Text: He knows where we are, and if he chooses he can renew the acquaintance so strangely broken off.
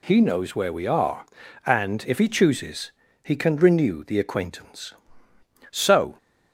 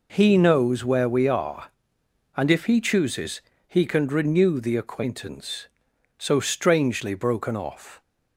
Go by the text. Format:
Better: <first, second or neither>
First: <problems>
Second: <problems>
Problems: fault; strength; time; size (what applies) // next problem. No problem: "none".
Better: second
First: pauses between "chooses" and "he"; slight; at 2.9 s; 0.32 s long // stops before "strangely broken off"; at 6.1 s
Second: pauses between "chooses" and "he"; slight; at 3.4 s; 0.28 s long